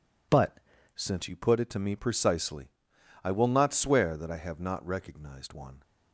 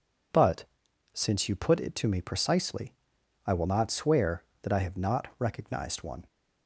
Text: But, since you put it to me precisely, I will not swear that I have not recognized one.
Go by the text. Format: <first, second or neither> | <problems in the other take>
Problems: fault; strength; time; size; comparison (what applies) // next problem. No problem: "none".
second | changes voice at "since"; from 0.9 s on; 4.9 s long